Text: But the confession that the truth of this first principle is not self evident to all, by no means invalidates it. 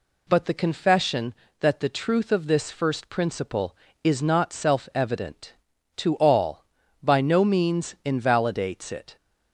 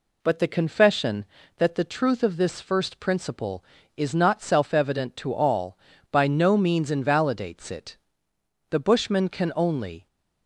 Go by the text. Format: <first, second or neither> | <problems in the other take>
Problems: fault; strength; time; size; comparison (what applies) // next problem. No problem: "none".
first | goes on to say "The Bushman can only"; from 8.6 s on; 1.3 s long